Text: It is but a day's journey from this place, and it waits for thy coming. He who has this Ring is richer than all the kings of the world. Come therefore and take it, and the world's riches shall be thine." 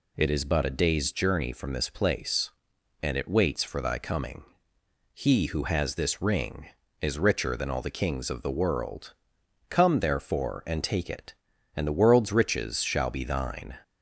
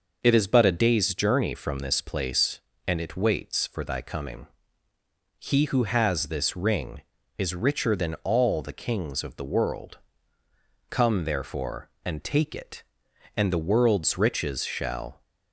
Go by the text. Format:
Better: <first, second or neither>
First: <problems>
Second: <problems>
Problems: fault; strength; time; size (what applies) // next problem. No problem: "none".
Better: first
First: none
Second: stops before "be thine"; at 15.2 s